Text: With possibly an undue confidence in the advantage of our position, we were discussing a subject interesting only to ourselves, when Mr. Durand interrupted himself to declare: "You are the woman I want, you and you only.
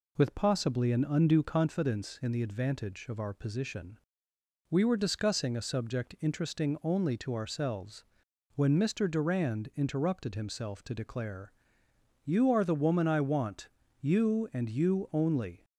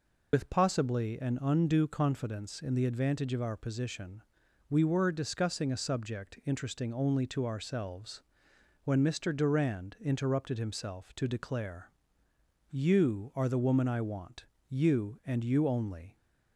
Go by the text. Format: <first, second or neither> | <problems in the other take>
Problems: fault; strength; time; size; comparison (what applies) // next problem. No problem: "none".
first | loses the start of "With"; at 0.3 s; 90 ms